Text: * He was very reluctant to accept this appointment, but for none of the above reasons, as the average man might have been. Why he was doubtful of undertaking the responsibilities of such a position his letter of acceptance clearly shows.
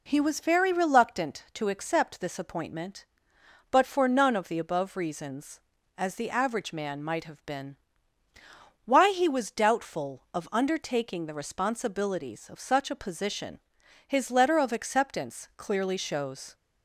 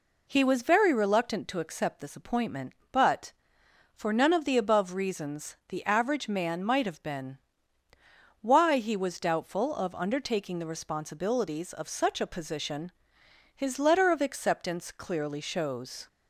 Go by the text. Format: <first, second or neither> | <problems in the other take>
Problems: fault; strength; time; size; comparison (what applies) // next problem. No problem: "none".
first | skips "as"; at 5.6 s // pauses between "position" and "his"; noticeable; at 12.9 s; 0.64 s long; noticeable in the first